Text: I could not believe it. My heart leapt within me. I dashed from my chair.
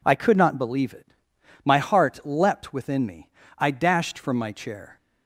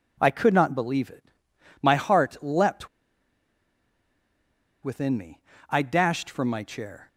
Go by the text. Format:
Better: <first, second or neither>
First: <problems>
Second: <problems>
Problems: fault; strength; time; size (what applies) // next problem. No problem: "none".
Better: first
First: none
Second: pauses between "leapt" and "within"; strong; at 2.8 s; 1.9 s long